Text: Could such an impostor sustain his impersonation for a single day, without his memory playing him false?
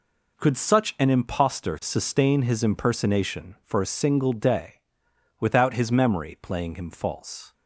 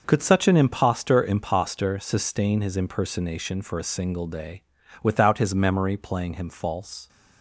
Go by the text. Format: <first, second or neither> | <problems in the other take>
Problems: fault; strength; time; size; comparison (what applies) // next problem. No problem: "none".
first | says "impostor" twice; at 1.2 s